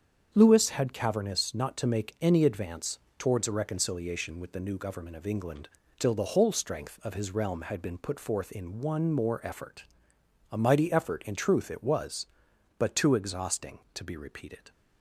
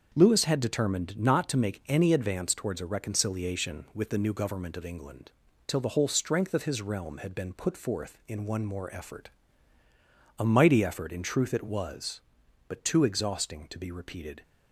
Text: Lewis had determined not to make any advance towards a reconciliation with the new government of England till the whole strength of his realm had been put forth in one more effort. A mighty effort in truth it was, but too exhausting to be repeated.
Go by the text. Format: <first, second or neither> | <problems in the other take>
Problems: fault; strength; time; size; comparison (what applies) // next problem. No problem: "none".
second | starts louder than the rest; strong; until 1.3 s; 7.5 dB; also in the second // says "cavernous" for "determined"; at 0.9 s // pauses between "advance" and "towards"; slight; at 2.9 s; 0.20 s long // pauses between "England" and "till"; slight; at 5.6 s; 0.32 s long; slight in the second